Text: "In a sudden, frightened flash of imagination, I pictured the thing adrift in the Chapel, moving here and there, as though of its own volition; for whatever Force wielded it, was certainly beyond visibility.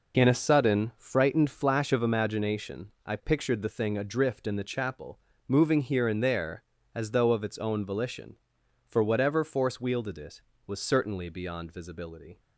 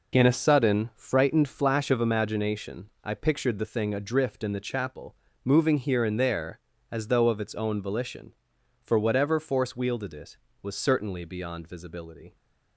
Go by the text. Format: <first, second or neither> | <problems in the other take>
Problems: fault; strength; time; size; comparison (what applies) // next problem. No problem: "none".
neither | none